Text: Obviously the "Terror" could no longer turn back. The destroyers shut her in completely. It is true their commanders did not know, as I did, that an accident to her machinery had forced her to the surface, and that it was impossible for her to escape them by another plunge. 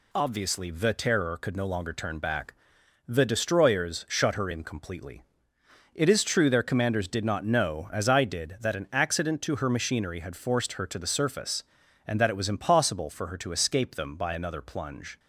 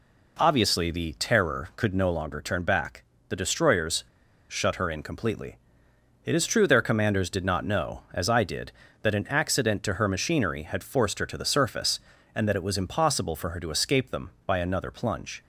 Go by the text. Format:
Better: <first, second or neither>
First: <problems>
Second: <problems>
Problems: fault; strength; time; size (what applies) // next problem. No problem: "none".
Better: first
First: none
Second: pauses between "destroyers" and "shut"; at 4.0 s; 0.45 s long